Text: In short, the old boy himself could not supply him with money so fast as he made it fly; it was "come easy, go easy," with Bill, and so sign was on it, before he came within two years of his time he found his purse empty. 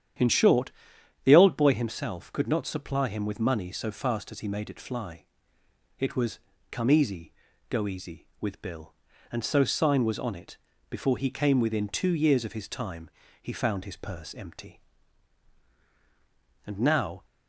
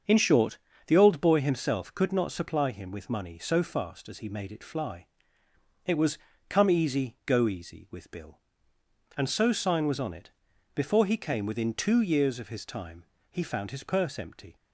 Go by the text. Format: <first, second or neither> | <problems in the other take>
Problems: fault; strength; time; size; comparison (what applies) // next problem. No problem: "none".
second | starts louder than the rest; strong; until 1.7 s; 9.5 dB; also in the second // pauses between "was" and "come"; slight; at 6.3 s; 0.32 s long; slight in the second // pauses between "time" and "he"; slight; at 13.1 s; 0.32 s long; slight in the second // goes on to say "And now"; from 16.6 s on; 0.60 s long